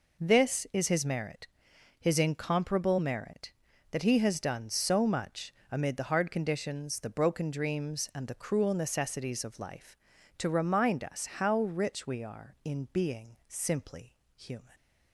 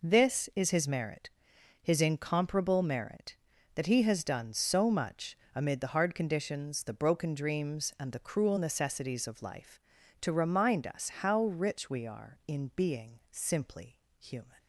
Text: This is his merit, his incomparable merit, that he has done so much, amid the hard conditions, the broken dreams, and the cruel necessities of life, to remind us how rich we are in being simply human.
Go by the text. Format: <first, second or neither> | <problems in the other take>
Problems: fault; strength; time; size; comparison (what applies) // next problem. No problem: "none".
neither | pauses between "simply" and "human"; slight; the same in both